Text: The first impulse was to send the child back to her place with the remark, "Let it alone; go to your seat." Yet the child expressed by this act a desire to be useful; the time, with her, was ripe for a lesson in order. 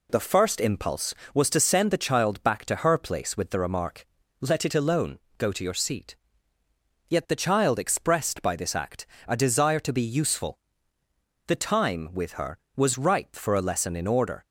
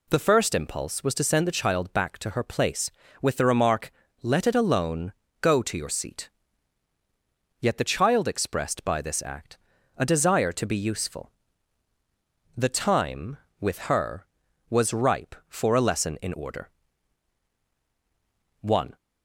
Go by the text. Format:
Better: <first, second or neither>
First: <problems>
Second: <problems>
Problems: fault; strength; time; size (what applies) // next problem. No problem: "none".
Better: first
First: pauses between "act" and "a"; slight; at 9.0 s; 0.20 s long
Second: pauses between "act" and "a"; at 9.5 s; 0.40 s long // goes on to say "One"; slight; from 18.6 s on; 0.34 s long